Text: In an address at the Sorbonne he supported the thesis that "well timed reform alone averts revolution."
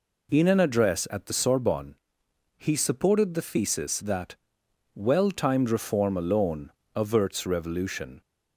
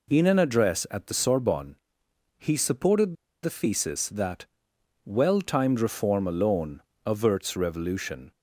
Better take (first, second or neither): first